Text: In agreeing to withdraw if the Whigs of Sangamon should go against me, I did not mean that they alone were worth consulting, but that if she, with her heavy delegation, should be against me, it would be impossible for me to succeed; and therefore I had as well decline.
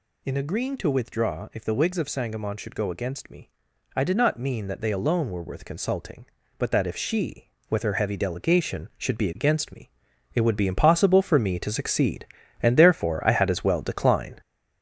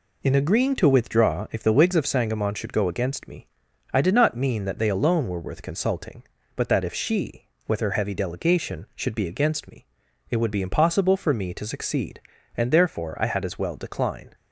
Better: second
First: gets louder; noticeable; throughout; 4.5 dB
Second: none

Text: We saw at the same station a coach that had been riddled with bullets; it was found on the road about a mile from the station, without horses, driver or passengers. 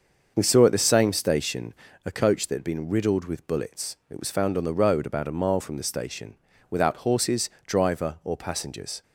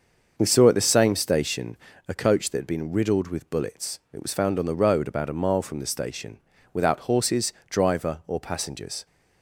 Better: neither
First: starts louder than the rest; until 1.3 s; 6.5 dB // pauses between "station" and "a"; slight; at 1.7 s; 0.30 s long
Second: starts louder than the rest; until 1.3 s; 6.5 dB // pauses between "station" and "a"; slight; at 1.7 s; 0.30 s long

